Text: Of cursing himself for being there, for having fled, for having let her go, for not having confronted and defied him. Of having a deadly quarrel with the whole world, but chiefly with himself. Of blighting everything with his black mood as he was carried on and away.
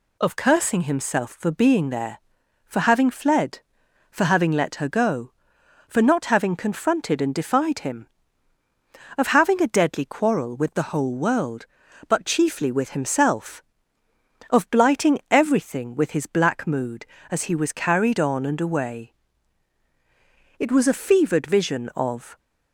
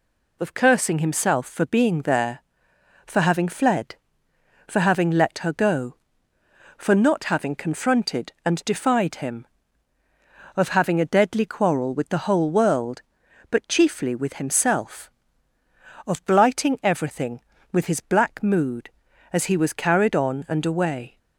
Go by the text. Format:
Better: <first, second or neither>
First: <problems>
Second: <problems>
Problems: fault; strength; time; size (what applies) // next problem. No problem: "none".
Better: second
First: goes on to say "It was a fevered vision of"; strong; from 20.5 s on; 1.8 s long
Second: none